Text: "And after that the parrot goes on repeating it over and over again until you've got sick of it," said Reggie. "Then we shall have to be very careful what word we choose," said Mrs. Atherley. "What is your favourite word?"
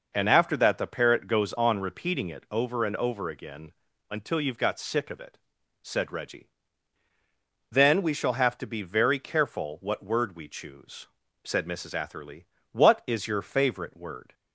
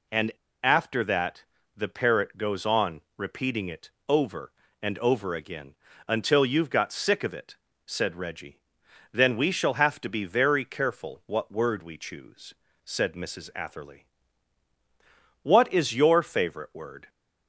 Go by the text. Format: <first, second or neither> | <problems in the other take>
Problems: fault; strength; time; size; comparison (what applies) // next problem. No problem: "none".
first | pauses between "And" and "after"; slight; at 0.3 s; 0.31 s long // pauses between "that" and "the"; slight; at 1.4 s; 0.34 s long // pauses between "on" and "repeating"; slight; at 3.0 s; 0.18 s long // pauses between "it" and "over"; slight; at 3.9 s; 0.18 s long // pauses between "again" and "until"; slight; at 5.7 s; 0.32 s long; also in the first